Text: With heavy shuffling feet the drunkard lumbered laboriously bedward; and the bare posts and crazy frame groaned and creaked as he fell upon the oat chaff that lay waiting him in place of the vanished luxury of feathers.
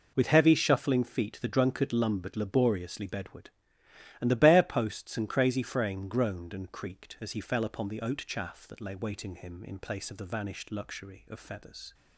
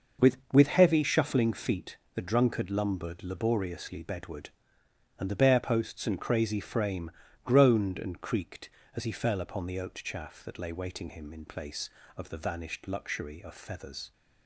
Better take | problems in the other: first | says "With" twice; at 0.5 s // pauses between "feet" and "the"; slight; at 1.9 s; 0.18 s long // pauses between "frame" and "groaned"; slight; at 7.1 s; 0.34 s long

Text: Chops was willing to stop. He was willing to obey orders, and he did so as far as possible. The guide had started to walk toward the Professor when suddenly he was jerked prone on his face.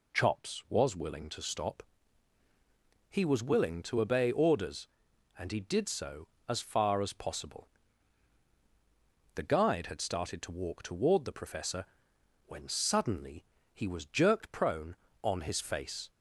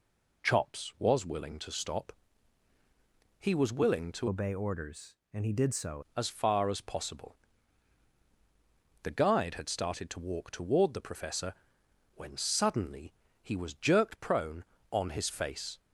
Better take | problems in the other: first | changes voice from "obey" to "so"; from 4.2 to 6.0 s; 1.8 s long // pauses between "Professor" and "when"; noticeable; at 11.5 s; 0.60 s long; noticeable in the first // pauses between "suddenly" and "he"; slight; at 13.1 s; 0.30 s long; slight in the first

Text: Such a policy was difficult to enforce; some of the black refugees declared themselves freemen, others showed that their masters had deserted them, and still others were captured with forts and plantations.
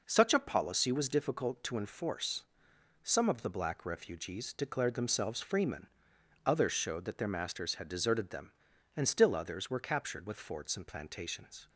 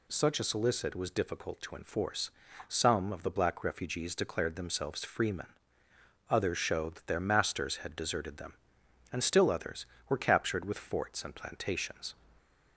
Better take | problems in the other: first | says "solicit" for "policy"; at 0.4 s

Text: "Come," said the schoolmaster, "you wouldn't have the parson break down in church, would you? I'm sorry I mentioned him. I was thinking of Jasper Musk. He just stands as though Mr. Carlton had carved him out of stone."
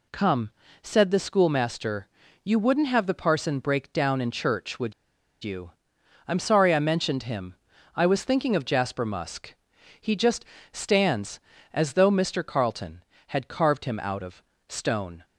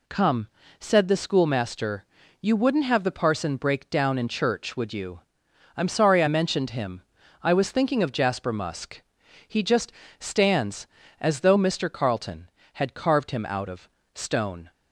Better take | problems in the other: second | pauses between "would" and "you"; noticeable; at 4.9 s; 0.51 s long // pauses between "just" and "stands"; slight; at 10.4 s; 0.26 s long; slight in the second // pauses between "of" and "stone"; slight; at 14.4 s; 0.24 s long; slight in the second

